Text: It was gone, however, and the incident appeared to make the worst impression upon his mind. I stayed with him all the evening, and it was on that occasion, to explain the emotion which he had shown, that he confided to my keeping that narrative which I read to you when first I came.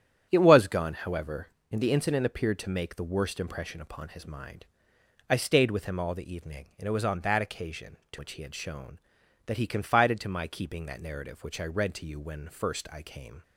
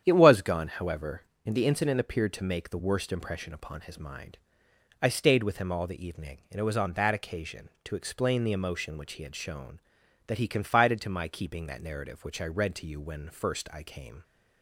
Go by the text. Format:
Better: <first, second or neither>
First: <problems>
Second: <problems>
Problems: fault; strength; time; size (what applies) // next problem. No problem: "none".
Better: second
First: starts louder than the rest; strong; until 1.3 s; 10 dB // skips "explain the emotion"; at 8.1 s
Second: starts louder than the rest; strong; until 1.0 s; 9 dB